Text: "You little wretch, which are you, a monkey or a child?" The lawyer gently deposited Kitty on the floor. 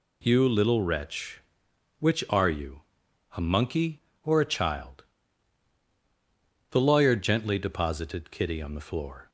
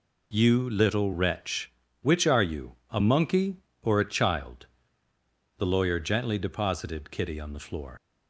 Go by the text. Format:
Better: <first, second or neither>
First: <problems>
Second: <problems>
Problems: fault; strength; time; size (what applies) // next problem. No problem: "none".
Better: first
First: none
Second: leaves "floor" unfinished; at 7.9 s; 90 ms